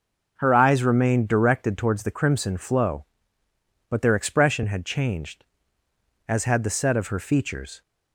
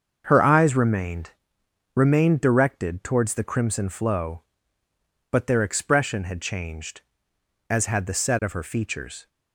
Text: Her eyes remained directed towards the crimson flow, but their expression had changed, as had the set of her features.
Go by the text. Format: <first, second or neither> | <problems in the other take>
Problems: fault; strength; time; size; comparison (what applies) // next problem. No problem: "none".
first | starts louder than the rest; until 1.2 s; 6.5 dB // says "remained" twice; at 1.9 s